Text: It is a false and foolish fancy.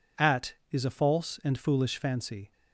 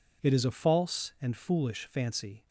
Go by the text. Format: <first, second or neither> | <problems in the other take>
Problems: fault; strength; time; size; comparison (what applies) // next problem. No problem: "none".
second | says "At" for "It"; at 0.1 s